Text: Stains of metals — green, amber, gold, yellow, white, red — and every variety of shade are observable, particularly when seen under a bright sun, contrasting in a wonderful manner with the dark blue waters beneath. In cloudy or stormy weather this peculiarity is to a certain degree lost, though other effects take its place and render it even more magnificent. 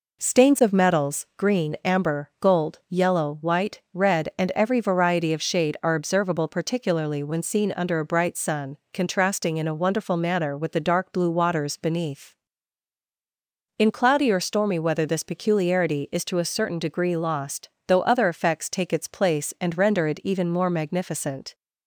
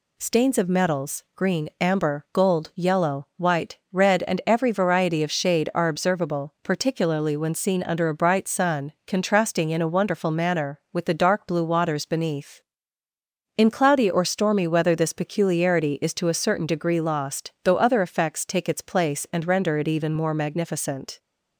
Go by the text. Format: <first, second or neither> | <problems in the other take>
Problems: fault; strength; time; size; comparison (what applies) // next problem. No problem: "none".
neither | none